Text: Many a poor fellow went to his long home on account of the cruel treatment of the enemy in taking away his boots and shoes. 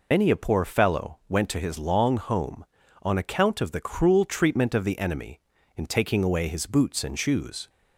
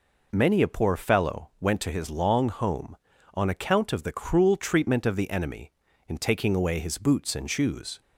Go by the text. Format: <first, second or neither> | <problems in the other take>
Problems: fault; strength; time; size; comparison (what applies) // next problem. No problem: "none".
second | loses the start of "Many"; at 0.1 s; 100 ms